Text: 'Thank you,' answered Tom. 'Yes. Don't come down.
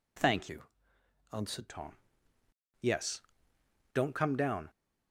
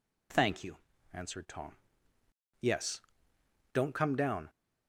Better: second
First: changes voice from "you" to "answered"; from 0.4 to 1.6 s; 1.2 s long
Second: none

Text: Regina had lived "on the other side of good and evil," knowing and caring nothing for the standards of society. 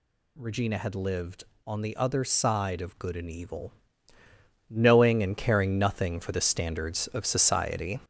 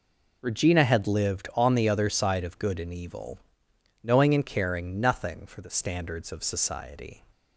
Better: second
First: gets louder; noticeable; throughout; 6 dB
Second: none

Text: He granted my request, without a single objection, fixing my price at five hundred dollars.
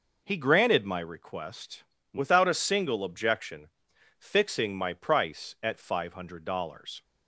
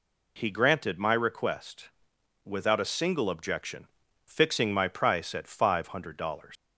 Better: first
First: none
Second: leaves "dollars" unfinished; at 6.5 s; 115 ms

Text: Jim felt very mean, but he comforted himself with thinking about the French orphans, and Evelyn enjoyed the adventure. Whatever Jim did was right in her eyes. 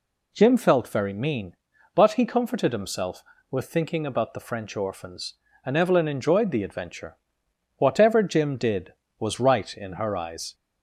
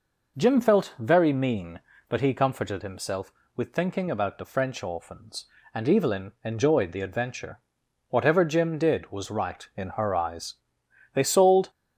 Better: first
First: none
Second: goes on to say "They sold"; from 11.1 s on; 0.56 s long

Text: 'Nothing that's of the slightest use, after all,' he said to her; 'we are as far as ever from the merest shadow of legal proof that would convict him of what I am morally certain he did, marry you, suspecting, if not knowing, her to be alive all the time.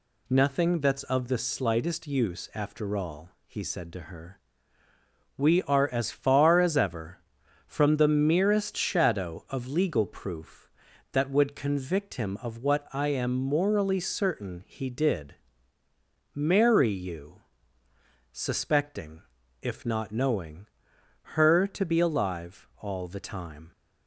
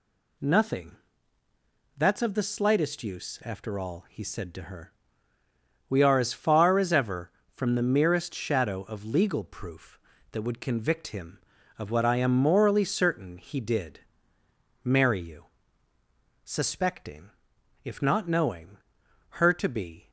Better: first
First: none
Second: pauses between "Nothing" and "that's"; at 0.9 s; 1.0 s long // stops before "alive all the time"; at 20.0 s

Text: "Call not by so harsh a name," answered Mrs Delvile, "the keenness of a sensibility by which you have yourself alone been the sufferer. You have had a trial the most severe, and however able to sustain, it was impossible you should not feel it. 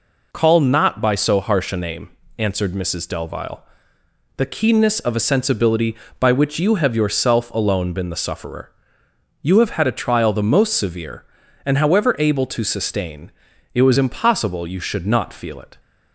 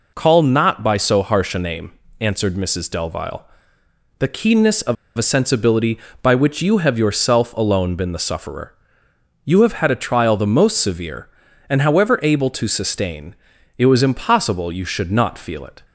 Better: first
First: none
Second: pauses between "of" and "a"; slight; at 4.9 s; 0.22 s long

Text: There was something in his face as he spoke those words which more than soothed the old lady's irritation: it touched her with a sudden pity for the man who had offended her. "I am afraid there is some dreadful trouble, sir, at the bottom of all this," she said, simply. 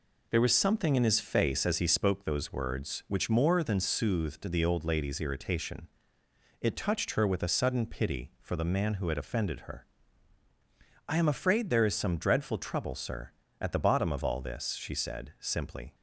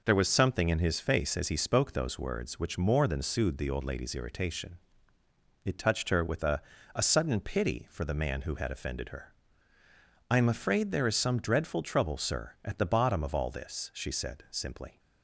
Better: first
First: none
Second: says "a" twice; at 6.9 s

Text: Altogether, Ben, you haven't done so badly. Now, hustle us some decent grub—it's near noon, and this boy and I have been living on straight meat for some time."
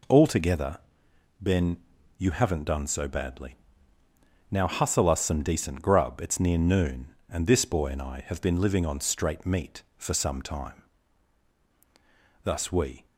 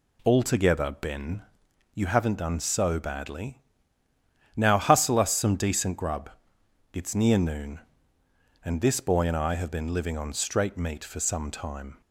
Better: second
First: goes on to say "Thus we"; noticeable; from 12.4 s on; 0.62 s long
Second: none

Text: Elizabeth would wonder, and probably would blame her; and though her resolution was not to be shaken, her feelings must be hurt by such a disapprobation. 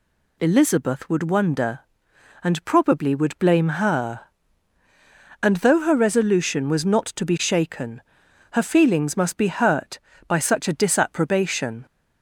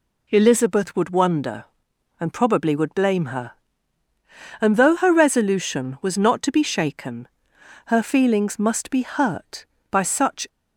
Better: first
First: none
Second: stops before "a disapprobation"; at 10.4 s

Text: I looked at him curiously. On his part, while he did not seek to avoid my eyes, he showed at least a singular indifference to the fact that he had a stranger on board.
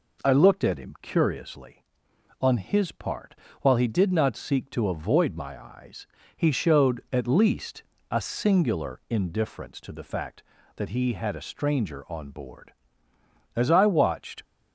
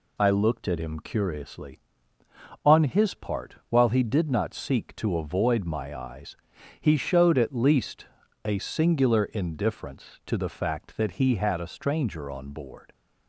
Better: second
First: pauses between "least" and "a"; slight; at 7.8 s; 0.28 s long // goes on to say "As I watched"; noticeable; from 13.5 s on; 0.88 s long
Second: pauses between "least" and "a"; at 8.0 s; 0.38 s long

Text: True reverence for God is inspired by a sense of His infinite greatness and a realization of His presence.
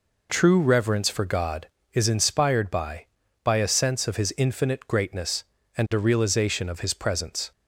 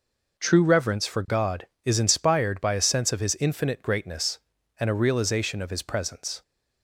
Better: second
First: says "by" twice; at 3.4 s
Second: none

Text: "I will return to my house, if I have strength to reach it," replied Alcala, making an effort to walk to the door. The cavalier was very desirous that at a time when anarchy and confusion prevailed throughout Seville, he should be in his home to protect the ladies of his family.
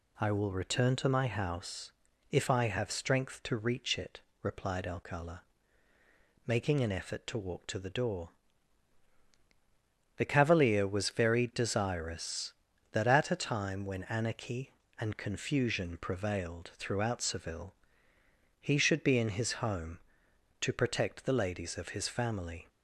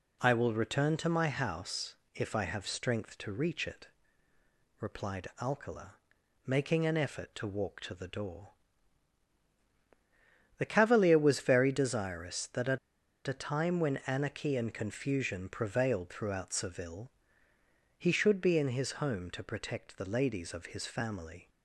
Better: first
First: none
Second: pauses between "at" and "a"; noticeable; at 12.7 s; 0.49 s long

